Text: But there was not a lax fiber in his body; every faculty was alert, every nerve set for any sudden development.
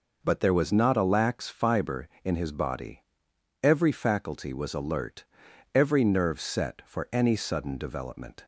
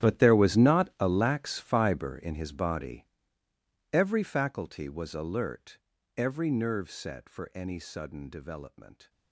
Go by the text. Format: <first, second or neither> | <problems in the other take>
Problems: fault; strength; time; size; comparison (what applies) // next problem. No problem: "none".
first | gets quieter; strong; throughout; 18 dB